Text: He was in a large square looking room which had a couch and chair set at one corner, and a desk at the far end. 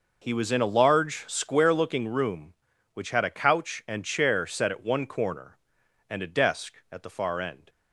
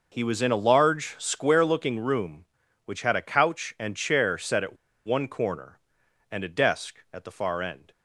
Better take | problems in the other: first | pauses between "at" and "one"; slight; at 4.7 s; 0.29 s long

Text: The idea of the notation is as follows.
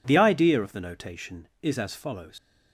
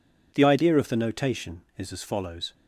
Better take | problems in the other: second | leaves "follows" unfinished; at 2.3 s; 80 ms

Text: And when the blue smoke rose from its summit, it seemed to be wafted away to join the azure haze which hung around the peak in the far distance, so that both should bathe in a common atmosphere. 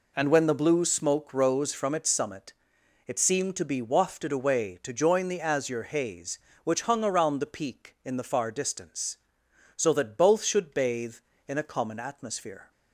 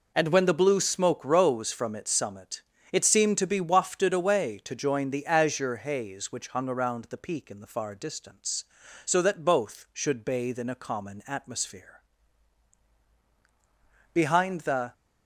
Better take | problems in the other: first | goes on to say "Behind the"; noticeable; from 14.1 s on; 0.80 s long

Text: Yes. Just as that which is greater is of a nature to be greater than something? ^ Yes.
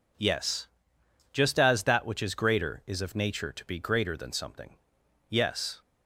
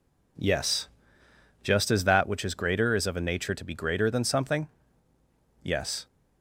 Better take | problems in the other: second | skips "a"; at 3.1 s

